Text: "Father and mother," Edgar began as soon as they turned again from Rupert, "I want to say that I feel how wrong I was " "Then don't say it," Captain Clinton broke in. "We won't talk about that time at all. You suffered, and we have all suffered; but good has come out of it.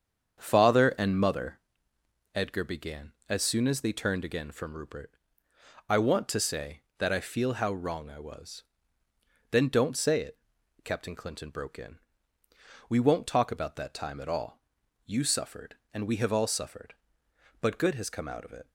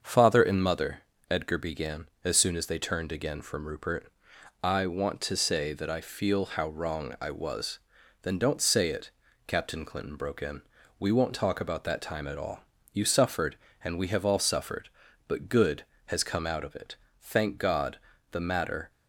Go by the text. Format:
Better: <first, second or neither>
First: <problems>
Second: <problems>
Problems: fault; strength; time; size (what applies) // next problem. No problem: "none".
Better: first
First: starts louder than the rest; strong; until 1.4 s; 7.5 dB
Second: starts louder than the rest; until 1.0 s; 6.5 dB // goes on to say "Thank God the matter"; strong; from 17.1 s on; 1.7 s long